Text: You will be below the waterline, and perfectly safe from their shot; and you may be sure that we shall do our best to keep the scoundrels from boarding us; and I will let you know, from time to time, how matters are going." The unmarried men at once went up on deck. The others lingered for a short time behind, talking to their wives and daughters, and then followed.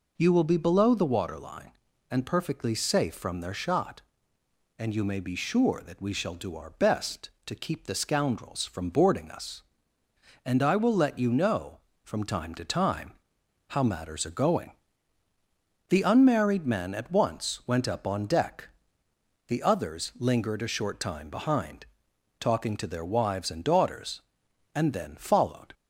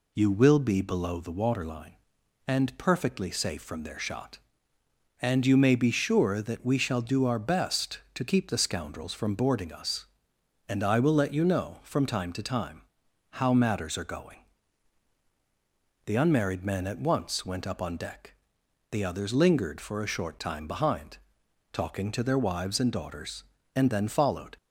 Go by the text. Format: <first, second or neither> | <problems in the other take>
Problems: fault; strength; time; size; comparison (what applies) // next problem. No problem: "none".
second | skips "for"; at 20.6 s